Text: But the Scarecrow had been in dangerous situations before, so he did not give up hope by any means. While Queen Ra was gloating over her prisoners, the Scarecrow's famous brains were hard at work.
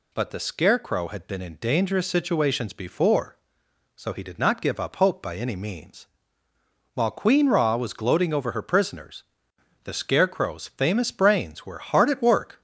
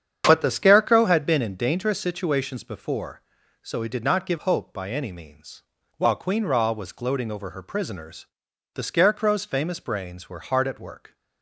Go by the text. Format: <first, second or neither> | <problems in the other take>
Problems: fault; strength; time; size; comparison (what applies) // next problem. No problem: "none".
first | starts louder than the rest; strong; until 1.2 s; 8.5 dB // skips "up"; at 4.3 s